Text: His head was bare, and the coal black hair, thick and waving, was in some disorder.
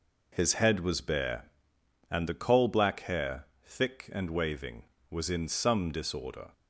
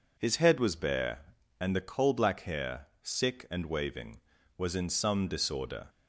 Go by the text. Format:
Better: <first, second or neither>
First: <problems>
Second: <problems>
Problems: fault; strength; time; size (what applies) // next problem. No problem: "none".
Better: first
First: none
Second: says "sick" for "thick"; at 3.0 s